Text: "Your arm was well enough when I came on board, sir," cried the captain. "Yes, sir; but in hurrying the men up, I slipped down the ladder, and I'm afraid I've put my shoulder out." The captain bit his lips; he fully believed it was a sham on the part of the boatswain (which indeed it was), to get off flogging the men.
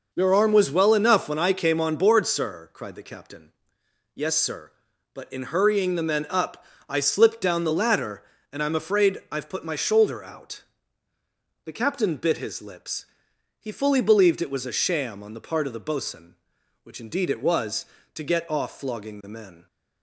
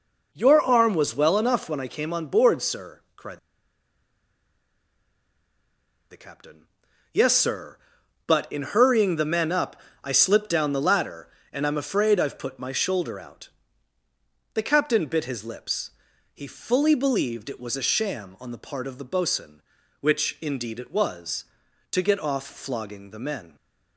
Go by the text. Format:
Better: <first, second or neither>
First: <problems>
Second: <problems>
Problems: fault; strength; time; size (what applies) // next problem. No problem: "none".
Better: first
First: none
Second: pauses between "cried" and "the"; strong; at 3.3 s; 2.7 s long